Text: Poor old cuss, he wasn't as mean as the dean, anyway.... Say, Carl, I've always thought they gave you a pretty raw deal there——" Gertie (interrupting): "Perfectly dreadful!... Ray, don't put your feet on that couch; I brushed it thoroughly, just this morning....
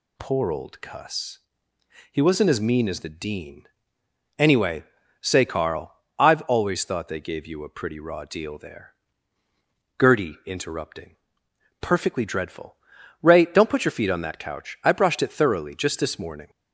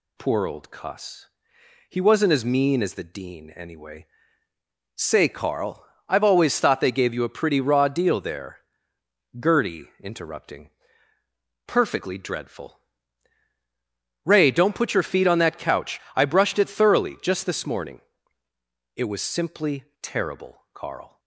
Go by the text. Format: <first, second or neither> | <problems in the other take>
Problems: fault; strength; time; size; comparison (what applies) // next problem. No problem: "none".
first | goes on to say "It was simply terrible Carl"; strong; from 18.9 s on; 2.2 s long